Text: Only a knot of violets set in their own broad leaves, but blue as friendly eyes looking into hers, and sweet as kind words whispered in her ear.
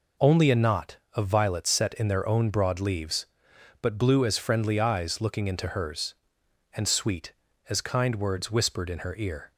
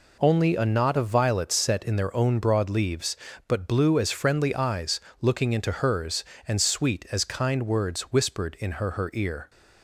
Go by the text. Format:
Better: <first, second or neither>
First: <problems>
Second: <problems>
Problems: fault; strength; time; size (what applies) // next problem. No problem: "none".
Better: first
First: none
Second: pauses between "eyes" and "looking"; slight; at 4.9 s; 0.22 s long // says "her" twice; at 8.9 s